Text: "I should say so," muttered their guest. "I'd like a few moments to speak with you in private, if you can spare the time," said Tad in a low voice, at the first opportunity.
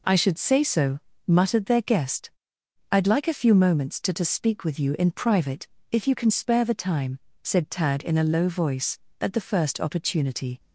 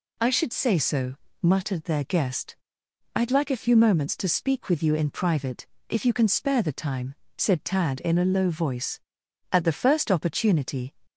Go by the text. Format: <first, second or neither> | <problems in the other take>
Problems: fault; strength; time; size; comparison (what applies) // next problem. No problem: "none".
second | says "to" twice; at 4.1 s